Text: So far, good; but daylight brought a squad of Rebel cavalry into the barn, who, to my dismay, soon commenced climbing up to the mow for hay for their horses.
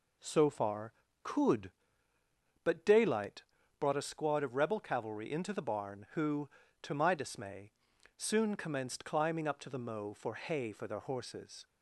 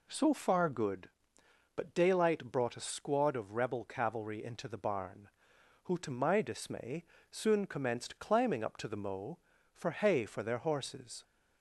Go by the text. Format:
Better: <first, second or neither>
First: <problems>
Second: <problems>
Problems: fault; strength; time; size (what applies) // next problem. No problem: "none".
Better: second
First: says "could" for "good"; at 1.2 s // pauses between "daylight" and "brought"; at 3.4 s; 0.38 s long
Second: none